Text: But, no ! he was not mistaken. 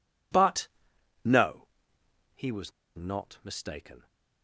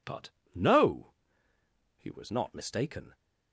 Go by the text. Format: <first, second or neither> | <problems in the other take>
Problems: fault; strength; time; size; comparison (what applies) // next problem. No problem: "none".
second | pauses between "was" and "not"; slight; at 2.7 s; 0.25 s long